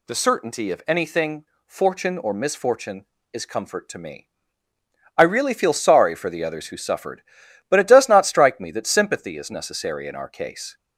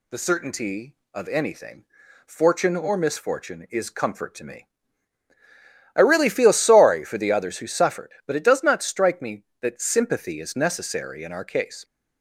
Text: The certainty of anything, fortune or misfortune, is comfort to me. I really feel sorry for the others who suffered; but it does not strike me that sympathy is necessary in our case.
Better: neither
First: none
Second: none

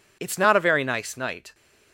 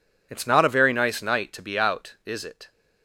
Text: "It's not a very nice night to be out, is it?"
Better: second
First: stops before "to be out is it"; at 1.5 s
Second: none

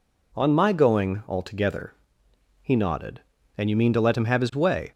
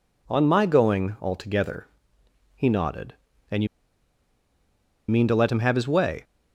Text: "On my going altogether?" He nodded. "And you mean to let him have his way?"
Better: first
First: none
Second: pauses between "you" and "mean"; strong; at 3.6 s; 1.4 s long

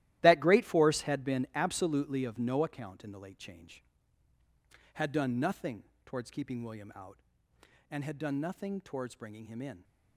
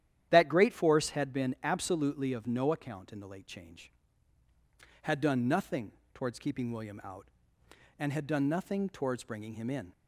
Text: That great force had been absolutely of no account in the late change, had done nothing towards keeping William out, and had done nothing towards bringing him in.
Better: second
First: gets quieter; strong; throughout; 13 dB // starts louder than the rest; strong; until 1.2 s; 14.5 dB // pauses between "nothing" and "towards"; slight; at 5.8 s; 0.22 s long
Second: starts louder than the rest; strong; until 1.3 s; 11 dB // pauses between "nothing" and "towards"; slight; at 5.9 s; 0.22 s long

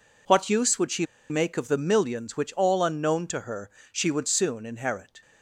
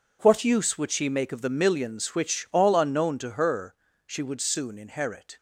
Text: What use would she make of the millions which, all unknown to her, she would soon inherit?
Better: second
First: pauses between "she" and "make"; slight; at 1.0 s; 0.24 s long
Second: none

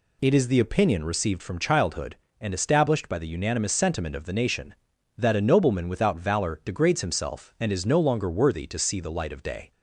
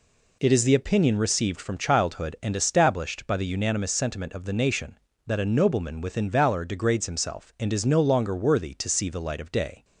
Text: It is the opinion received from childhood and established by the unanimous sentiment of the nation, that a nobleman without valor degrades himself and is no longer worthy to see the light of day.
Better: first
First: none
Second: says "within" for "without"; at 6.0 s

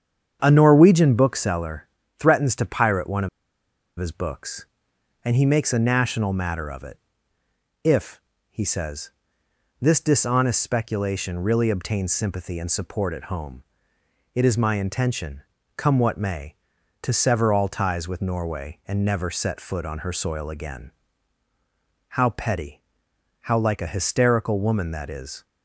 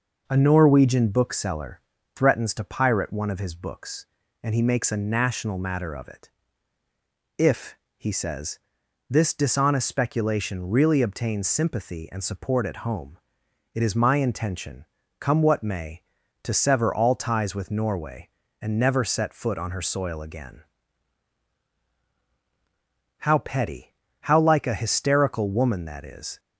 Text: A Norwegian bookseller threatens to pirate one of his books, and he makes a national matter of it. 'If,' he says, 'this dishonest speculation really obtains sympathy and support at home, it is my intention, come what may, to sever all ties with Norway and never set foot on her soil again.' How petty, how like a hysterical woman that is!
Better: second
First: starts louder than the rest; strong; until 1.4 s; 8 dB // pauses between "bookseller" and "threatens"; slight; at 1.8 s; 0.32 s long // pauses between "of" and "his"; noticeable; at 3.2 s; 0.70 s long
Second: pauses between "bookseller" and "threatens"; slight; at 1.8 s; 0.34 s long

